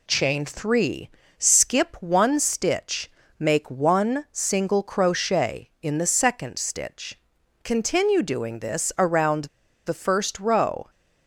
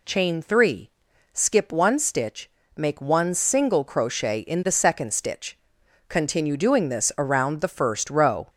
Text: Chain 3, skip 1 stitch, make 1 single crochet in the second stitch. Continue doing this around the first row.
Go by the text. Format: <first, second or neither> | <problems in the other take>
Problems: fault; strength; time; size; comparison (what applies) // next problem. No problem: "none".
second | pauses between "around" and "the"; at 9.4 s; 0.40 s long